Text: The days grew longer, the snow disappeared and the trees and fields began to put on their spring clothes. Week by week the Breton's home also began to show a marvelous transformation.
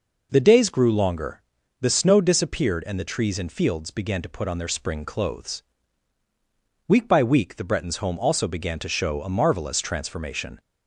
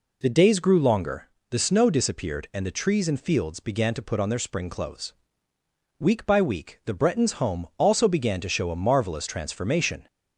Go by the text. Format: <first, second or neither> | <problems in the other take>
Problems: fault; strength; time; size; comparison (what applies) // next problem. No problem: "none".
neither | none